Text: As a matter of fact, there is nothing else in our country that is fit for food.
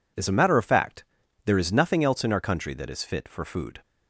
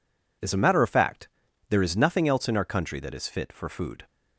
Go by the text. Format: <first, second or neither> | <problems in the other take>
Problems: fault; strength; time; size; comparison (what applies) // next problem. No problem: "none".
neither | none